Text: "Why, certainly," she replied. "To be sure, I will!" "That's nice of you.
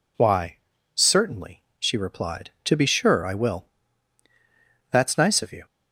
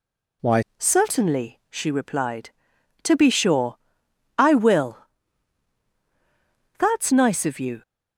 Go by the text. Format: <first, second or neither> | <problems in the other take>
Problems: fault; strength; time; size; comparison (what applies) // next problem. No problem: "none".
first | changes voice at "certainly"; from 0.7 s on; 7.1 s long